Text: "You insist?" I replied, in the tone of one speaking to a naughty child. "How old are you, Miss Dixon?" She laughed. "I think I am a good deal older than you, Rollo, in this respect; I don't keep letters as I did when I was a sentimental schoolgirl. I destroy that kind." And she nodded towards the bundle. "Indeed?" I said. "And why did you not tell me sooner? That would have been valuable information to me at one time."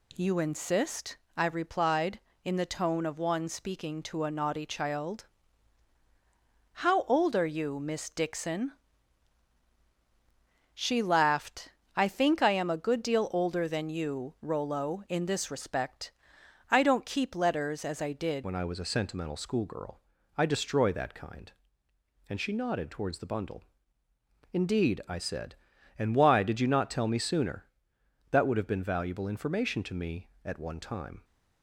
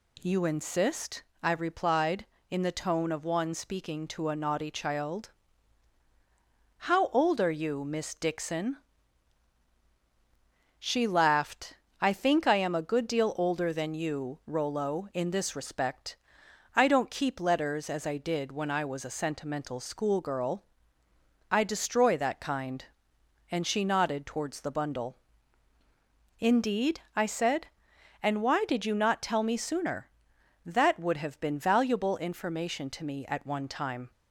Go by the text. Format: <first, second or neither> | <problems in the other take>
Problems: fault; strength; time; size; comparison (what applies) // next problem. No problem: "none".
second | changes voice at "when"; from 18.4 s on; 12.8 s long